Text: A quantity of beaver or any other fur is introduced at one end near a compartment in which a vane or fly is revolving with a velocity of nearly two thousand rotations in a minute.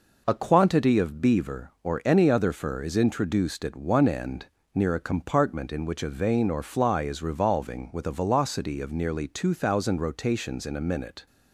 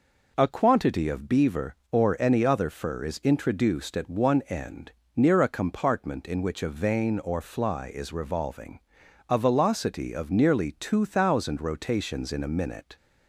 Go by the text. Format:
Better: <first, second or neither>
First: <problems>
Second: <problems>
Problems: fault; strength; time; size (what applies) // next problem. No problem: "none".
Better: first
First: pauses between "end" and "near"; slight; at 4.4 s; 0.28 s long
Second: pauses between "end" and "near"; slight; at 4.8 s; 0.26 s long // skips "with"; at 9.0 s